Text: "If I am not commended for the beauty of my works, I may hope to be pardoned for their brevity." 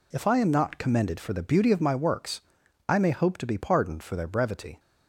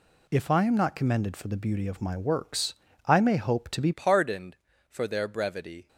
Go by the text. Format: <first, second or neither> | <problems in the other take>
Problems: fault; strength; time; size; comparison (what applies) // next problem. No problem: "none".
first | changes voice at "pardoned"; from 3.9 s on; 1.9 s long